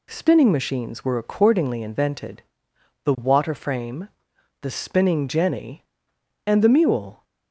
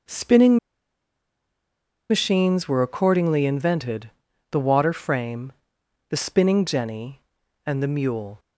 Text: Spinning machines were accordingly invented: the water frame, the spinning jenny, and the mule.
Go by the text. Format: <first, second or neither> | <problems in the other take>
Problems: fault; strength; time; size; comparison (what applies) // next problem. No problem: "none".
first | pauses between "Spinning" and "machines"; strong; at 0.5 s; 1.5 s long